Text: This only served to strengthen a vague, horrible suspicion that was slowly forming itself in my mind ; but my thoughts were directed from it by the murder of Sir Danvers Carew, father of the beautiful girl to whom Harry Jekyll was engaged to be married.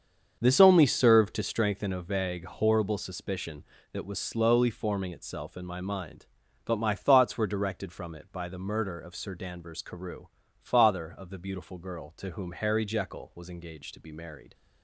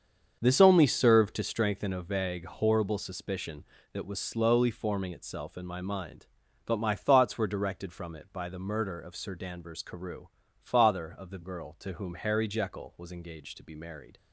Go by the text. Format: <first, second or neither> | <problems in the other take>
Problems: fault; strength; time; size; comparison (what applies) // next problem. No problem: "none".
first | starts louder than the rest; until 1.4 s; 7 dB; also in the first // skips "beautiful"; at 11.4 s